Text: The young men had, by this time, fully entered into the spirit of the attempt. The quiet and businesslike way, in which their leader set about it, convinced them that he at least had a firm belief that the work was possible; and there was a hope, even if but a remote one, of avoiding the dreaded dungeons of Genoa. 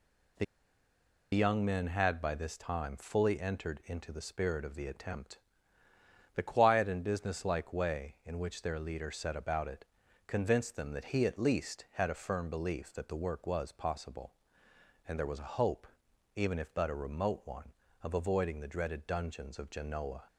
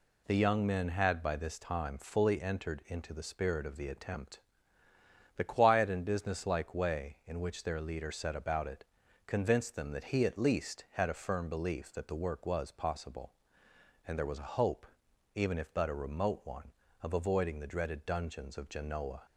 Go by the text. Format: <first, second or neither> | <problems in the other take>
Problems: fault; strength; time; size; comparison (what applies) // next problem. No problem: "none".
second | pauses between "The" and "young"; noticeable; at 0.4 s; 0.88 s long